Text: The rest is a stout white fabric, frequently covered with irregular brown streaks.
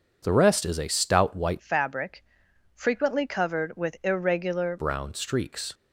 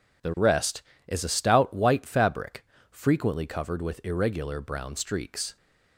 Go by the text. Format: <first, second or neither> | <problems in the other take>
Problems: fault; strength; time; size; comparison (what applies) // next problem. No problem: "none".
second | changes voice from "fabric" to "irregular"; from 1.5 to 4.7 s; 3.2 s long